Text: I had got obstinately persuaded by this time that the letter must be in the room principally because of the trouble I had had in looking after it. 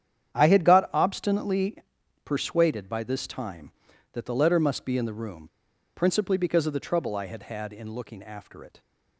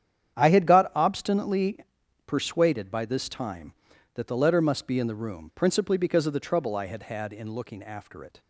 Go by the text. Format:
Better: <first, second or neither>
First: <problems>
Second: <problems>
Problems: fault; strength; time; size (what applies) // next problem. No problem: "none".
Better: second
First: starts louder than the rest; strong; until 1.3 s; 9 dB // pauses between "obstinately" and "persuaded"; noticeable; at 1.7 s; 0.48 s long // pauses between "room" and "principally"; noticeable; at 5.4 s; 0.47 s long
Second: starts louder than the rest; strong; until 1.4 s; 9 dB // pauses between "obstinately" and "persuaded"; noticeable; at 1.7 s; 0.48 s long